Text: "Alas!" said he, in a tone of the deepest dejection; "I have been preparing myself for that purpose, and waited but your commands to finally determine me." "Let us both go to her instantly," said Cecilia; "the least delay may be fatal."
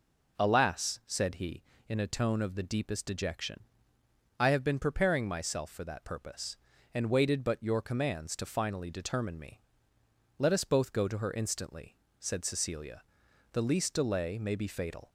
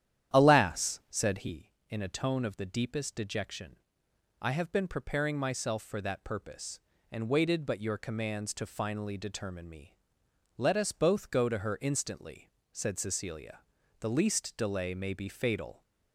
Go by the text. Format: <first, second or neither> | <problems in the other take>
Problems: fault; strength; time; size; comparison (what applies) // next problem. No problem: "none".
first | starts louder than the rest; strong; until 1.6 s; 10.5 dB